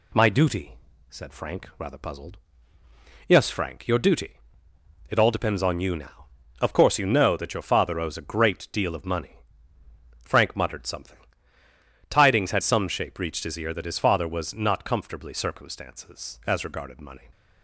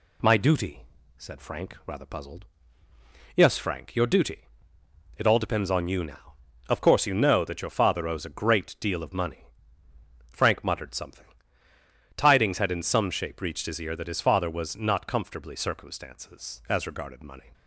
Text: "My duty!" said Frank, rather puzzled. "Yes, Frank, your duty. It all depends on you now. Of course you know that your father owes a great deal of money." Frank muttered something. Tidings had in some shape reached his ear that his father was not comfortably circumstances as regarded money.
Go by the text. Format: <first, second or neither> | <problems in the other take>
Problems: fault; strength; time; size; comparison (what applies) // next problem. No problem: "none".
second | skips "in"; at 12.6 s